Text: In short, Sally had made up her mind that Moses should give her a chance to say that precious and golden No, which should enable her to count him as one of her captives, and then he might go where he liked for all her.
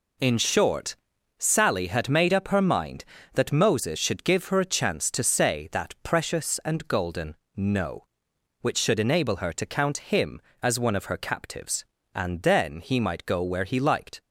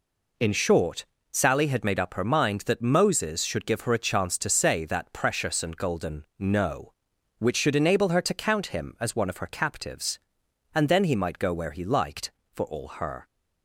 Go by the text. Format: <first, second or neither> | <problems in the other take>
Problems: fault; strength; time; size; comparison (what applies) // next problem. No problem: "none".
second | pauses between "golden" and "No"; slight; at 7.3 s; 0.22 s long // stops before "for all her"; at 14.2 s